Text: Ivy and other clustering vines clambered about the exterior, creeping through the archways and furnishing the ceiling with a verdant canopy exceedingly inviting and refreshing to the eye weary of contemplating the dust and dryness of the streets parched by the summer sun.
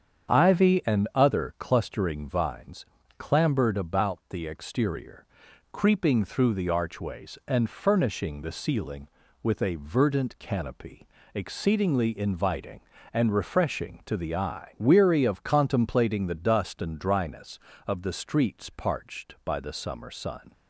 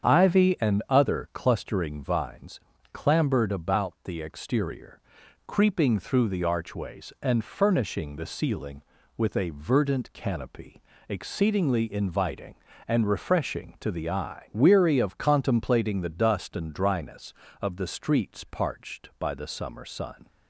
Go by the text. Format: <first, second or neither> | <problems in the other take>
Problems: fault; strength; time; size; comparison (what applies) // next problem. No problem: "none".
neither | starts louder than the rest; strong; the same in both // pauses between "vines" and "clambered"; slight; the same in both // pauses between "canopy" and "exceedingly"; slight; the same in both